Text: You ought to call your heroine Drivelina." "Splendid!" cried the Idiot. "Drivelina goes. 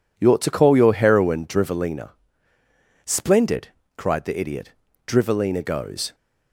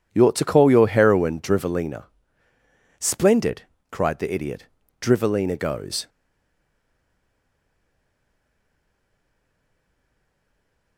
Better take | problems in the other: first | stays silent after the last word; strong; from 6.0 s on; 4.9 s long

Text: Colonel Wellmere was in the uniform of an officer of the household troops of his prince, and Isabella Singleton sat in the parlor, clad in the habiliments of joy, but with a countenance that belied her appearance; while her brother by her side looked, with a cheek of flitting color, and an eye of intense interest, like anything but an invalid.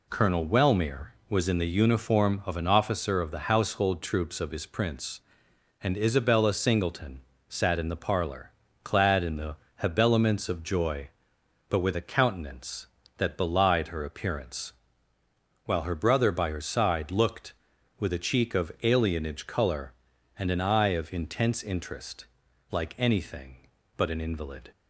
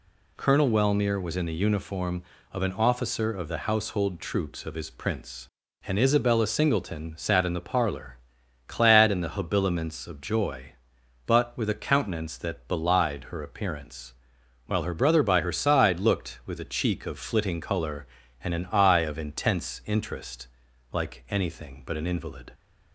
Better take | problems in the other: second | pauses between "Singleton" and "sat"; slight; at 7.2 s; 0.26 s long // pauses between "the" and "habiliments"; slight; at 9.5 s; 0.22 s long // says "alienage" for "flitting"; at 18.8 s

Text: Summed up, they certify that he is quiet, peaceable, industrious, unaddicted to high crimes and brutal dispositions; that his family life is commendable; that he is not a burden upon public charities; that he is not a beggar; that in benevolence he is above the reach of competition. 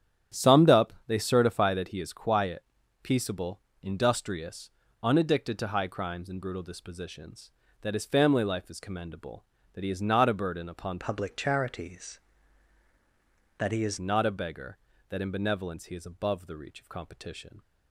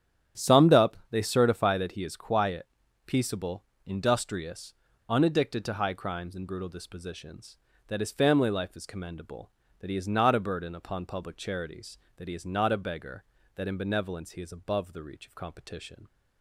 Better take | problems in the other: second | starts louder than the rest; strong; until 1.4 s; 10 dB; strong in the second // changes voice from "public" to "is"; from 10.9 to 13.9 s; 3.0 s long

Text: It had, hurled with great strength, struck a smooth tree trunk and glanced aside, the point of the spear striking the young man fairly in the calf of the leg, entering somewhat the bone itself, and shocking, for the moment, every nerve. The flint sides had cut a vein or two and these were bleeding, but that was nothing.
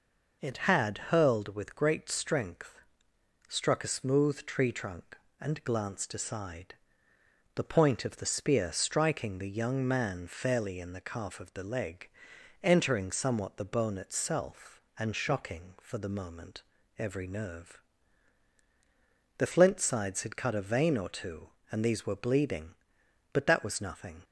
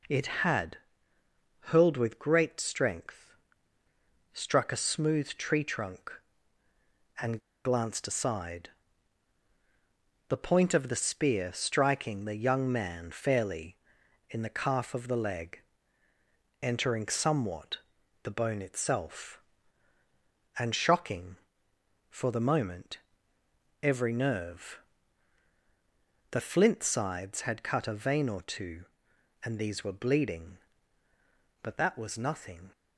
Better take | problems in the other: first | pauses between "and" and "glanced"; slight; at 7.3 s; 0.24 s long // pauses between "somewhat" and "the"; noticeable; at 17.7 s; 0.46 s long

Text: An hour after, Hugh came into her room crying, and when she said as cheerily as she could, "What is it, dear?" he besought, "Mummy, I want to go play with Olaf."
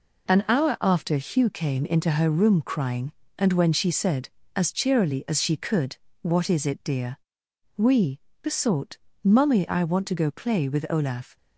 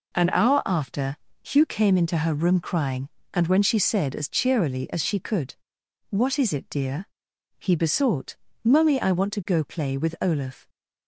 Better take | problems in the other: second | says "we" for "he"; at 7.7 s

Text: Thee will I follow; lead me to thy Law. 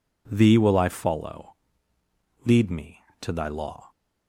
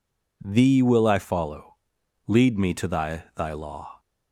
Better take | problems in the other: first | says "thy" twice; at 3.3 s

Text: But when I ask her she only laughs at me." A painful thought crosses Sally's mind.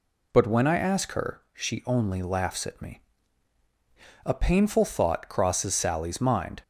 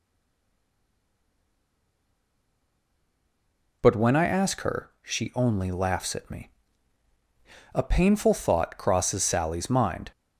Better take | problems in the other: first | stays silent before the first word; strong; until 3.8 s; 3.8 s long

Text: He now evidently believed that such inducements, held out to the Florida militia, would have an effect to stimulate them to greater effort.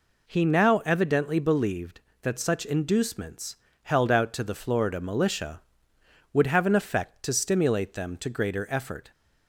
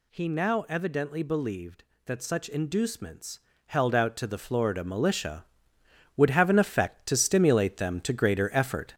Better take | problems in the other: first | gets louder; noticeable; throughout; 5.5 dB

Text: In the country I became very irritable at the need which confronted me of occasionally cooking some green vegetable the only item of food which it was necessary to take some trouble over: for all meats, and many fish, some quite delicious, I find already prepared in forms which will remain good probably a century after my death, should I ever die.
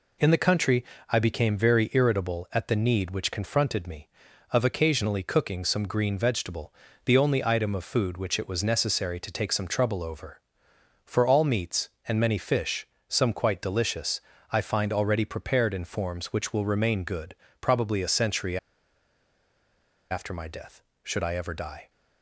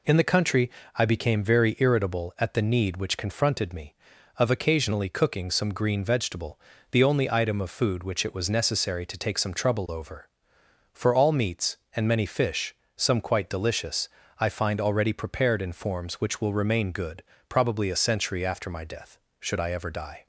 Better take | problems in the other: second | pauses between "country" and "I"; slight; at 0.8 s; 0.26 s long; slight in the second // pauses between "vegetable" and "the"; slight; at 6.7 s; 0.32 s long; slight in the second // pauses between "good" and "probably"; slight; at 17.3 s; 0.24 s long; slight in the second // pauses between "century" and "after"; strong; at 18.5 s; 1.5 s long

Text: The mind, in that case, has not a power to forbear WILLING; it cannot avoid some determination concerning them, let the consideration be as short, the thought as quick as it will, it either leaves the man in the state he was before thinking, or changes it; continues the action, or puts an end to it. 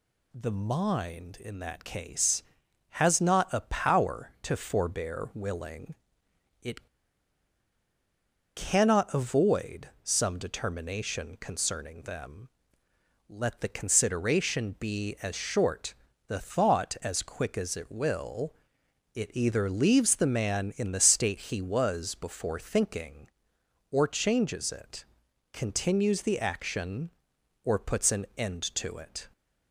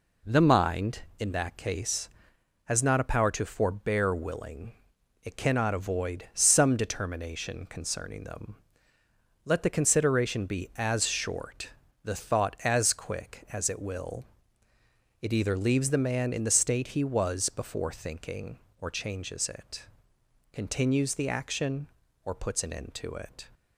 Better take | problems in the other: second | pauses between "it" and "cannot"; strong; at 6.8 s; 1.6 s long // pauses between "avoid" and "some"; slight; at 9.8 s; 0.16 s long

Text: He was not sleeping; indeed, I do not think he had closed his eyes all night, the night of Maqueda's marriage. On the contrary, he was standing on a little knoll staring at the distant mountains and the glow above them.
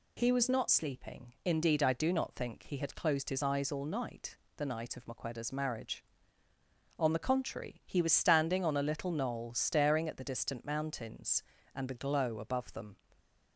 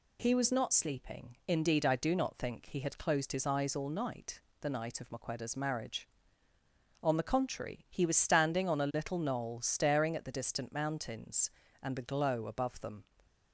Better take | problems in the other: neither | none

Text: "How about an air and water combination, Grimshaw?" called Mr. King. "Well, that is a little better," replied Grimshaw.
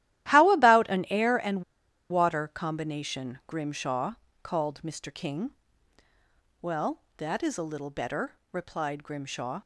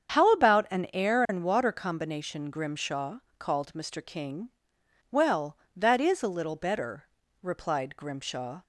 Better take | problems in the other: second | starts louder than the rest; strong; until 1.3 s; 13.5 dB; strong in the second // pauses between "and" and "water"; noticeable; at 1.6 s; 0.47 s long

